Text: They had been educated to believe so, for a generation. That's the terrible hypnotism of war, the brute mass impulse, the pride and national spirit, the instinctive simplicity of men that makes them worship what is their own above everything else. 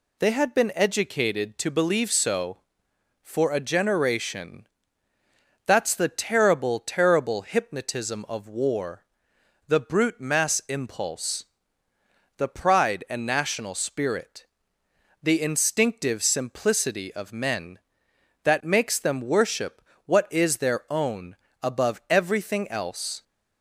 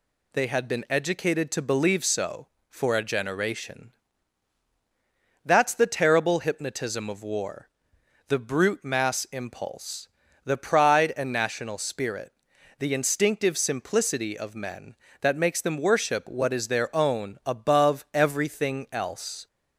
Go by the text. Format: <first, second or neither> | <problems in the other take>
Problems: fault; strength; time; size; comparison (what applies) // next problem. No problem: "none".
second | says "terrible" twice; at 6.7 s // pauses between "worship" and "what"; slight; at 19.8 s; 0.24 s long // pauses between "own" and "above"; slight; at 21.3 s; 0.26 s long